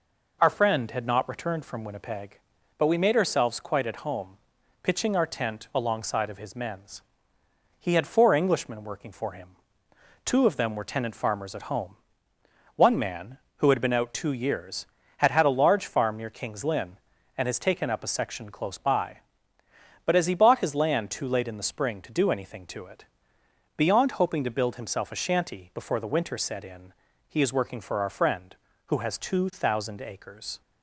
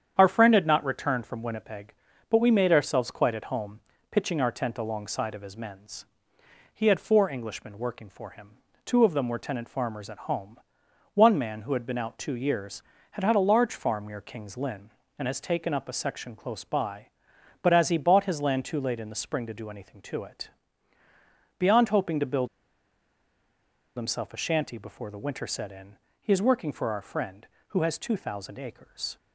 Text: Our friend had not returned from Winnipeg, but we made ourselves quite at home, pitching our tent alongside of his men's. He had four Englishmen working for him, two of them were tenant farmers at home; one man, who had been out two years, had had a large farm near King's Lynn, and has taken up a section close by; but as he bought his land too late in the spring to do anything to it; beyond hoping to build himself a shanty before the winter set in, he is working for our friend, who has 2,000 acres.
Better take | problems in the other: first | starts louder than the rest; strong; until 1.1 s; 8.5 dB // pauses between "build" and "himself"; strong; at 22.4 s; 1.4 s long

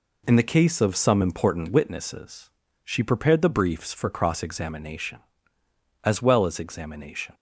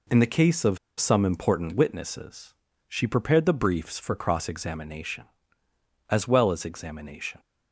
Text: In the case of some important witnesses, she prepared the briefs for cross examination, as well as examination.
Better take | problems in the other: first | pauses between "of" and "some"; slight; at 0.7 s; 0.21 s long

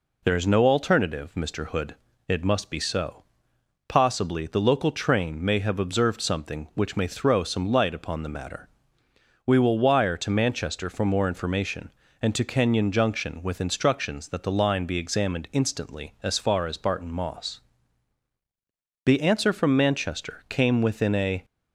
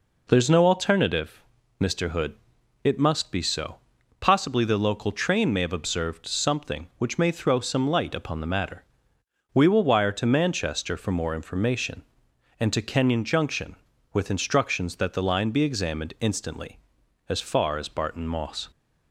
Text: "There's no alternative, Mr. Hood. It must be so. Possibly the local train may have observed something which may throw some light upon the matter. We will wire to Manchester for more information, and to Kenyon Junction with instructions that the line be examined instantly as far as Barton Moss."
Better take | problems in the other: second | goes on to say "The answer from Manchester came within a"; strong; from 19.0 s on; 2.4 s long

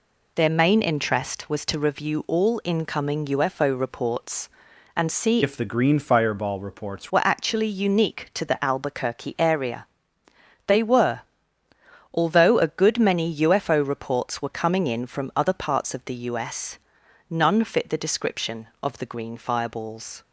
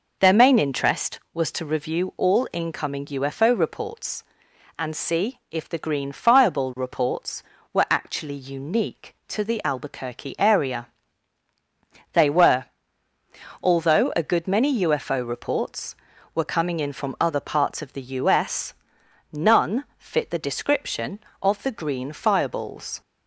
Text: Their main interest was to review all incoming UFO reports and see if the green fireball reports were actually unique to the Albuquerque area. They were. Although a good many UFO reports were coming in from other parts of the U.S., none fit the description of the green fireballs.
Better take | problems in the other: second | changes voice from "if" to "reports"; from 5.4 to 7.1 s; 1.7 s long

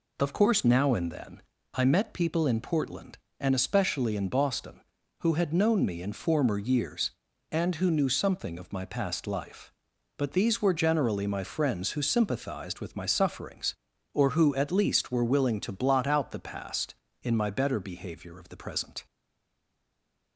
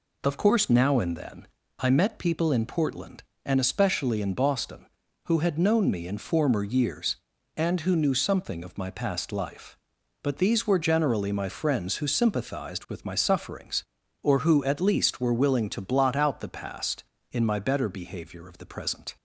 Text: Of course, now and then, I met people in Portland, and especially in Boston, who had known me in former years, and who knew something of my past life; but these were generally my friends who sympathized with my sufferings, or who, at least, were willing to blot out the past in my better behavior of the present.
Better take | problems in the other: second | stays silent after the last word; noticeable; from 19.0 s on; 1.3 s long

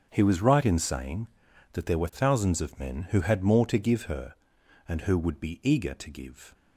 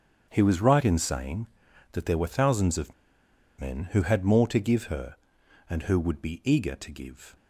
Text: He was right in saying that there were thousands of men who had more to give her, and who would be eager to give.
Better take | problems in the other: first | starts louder than the rest; strong; until 1.3 s; 7.5 dB; strong in the first // pauses between "of" and "men"; noticeable; at 2.9 s; 0.65 s long

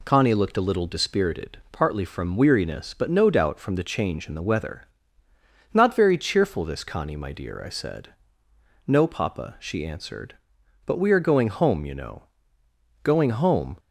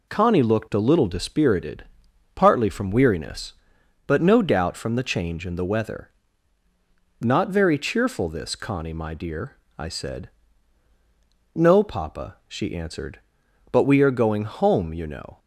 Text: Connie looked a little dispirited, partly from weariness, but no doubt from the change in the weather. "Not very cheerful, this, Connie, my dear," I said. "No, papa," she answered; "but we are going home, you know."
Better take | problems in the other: second | goes on to say "Going home"; noticeable; from 13.0 s on; 0.74 s long

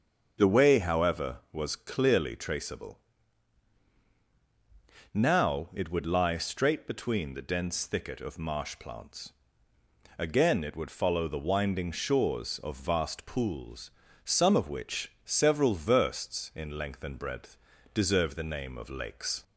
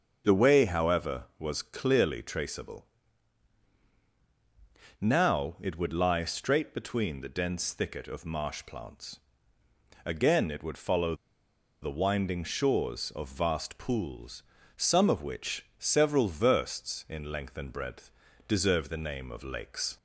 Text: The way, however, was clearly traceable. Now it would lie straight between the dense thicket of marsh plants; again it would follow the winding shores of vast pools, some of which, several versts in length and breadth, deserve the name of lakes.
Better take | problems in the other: first | starts louder than the rest; until 1.2 s; 6.5 dB; also in the first // pauses between "follow" and "the"; noticeable; at 11.1 s; 0.68 s long

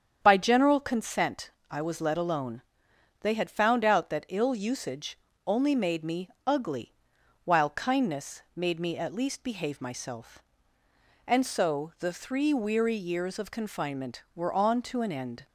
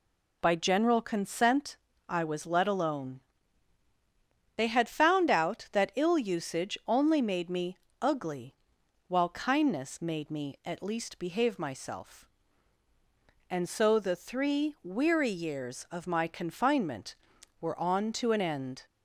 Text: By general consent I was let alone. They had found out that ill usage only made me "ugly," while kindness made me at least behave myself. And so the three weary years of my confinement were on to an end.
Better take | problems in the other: second | starts louder than the rest; strong; until 1.2 s; 8 dB // pauses between "consent" and "I"; slight; at 1.4 s; 0.22 s long; slight in the second // pauses between "usage" and "only"; slight; at 5.1 s; 0.30 s long // pauses between "me" and "ugly"; slight; at 6.2 s; 0.16 s long; slight in the second // skips "my"; at 13.4 s

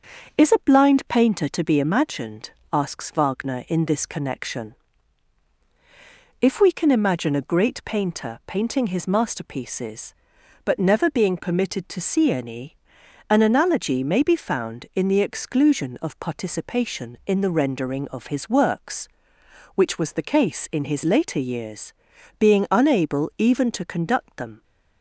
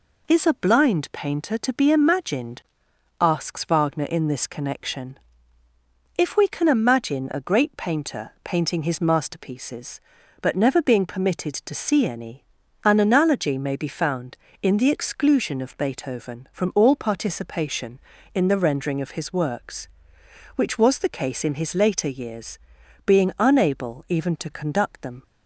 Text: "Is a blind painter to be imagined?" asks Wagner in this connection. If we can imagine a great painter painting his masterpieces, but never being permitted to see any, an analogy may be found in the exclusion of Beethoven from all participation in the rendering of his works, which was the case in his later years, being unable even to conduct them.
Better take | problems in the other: second | skips "Beethoven from all"; at 16.1 s

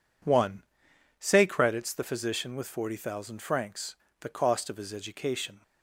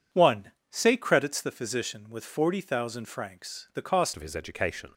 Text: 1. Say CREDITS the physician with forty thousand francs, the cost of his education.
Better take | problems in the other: first | changes voice at "of"; from 4.1 s on; 0.8 s long

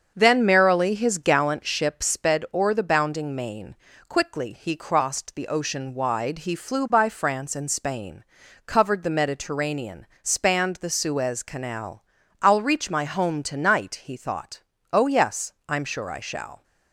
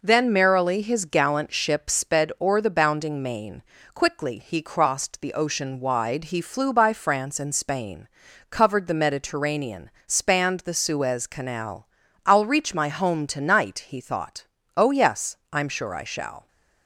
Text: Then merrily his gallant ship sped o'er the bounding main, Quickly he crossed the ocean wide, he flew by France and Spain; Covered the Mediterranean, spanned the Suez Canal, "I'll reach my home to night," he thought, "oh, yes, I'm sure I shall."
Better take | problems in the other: second | starts louder than the rest; until 1.6 s; 7 dB

